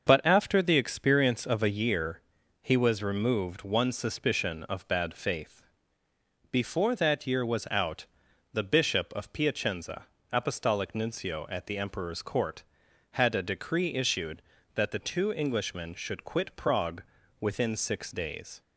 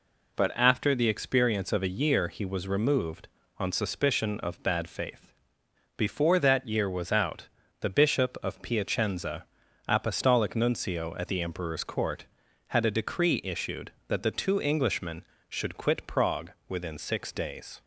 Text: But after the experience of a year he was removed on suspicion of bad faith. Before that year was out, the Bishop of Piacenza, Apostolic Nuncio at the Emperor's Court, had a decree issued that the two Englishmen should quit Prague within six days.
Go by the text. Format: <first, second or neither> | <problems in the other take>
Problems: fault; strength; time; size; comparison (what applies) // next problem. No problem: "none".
second | starts louder than the rest; until 1.1 s; 6.5 dB // pauses between "year" and "he"; at 2.2 s; 0.40 s long // says "one" for "on"; at 3.6 s // pauses between "Prague" and "within"; at 17.0 s; 0.38 s long